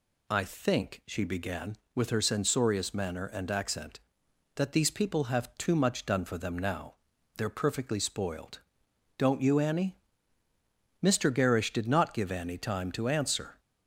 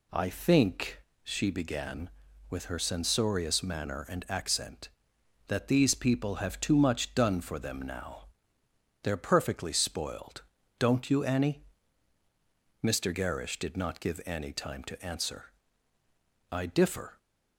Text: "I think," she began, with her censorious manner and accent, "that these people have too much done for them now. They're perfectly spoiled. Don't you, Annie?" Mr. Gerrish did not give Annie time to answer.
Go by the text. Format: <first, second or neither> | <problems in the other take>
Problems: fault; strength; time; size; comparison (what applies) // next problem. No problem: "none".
first | goes on to say "I differ"; noticeable; from 16.4 s on; 0.68 s long